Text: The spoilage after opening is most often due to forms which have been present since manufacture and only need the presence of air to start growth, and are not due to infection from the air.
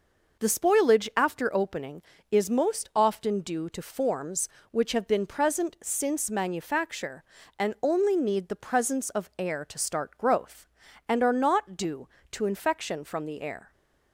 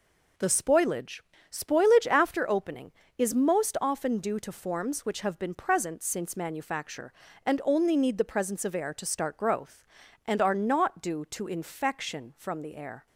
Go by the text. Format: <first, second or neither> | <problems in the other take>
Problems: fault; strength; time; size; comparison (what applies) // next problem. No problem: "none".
first | says "spoilage" twice; at 1.4 s